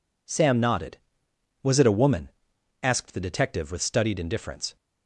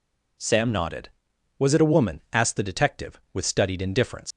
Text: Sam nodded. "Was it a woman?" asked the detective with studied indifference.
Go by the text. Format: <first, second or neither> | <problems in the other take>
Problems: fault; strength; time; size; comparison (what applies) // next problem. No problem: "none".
first | leaves "indifference" unfinished; at 4.3 s; 80 ms